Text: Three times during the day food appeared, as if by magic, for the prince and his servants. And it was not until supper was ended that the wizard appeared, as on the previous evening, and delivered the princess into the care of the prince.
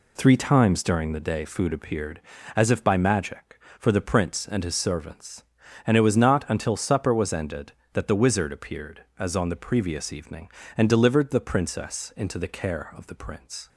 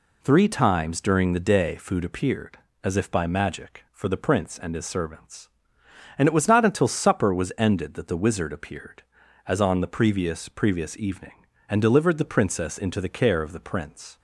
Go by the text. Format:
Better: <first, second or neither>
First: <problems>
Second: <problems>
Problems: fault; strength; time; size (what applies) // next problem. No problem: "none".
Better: first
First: none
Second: says "previous" twice; at 10.4 s